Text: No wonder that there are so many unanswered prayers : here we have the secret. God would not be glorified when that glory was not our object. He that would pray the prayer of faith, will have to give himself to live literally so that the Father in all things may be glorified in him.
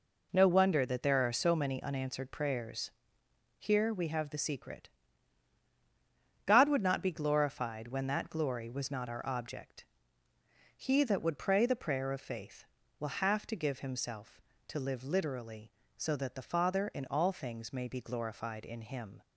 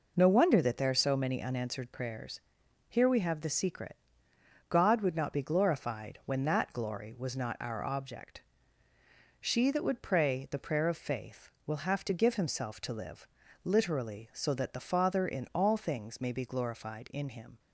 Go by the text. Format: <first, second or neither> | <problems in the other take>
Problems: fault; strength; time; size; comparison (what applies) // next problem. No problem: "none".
first | says "She" for "He"; at 9.4 s // pauses between "live" and "literally"; at 13.2 s; 0.38 s long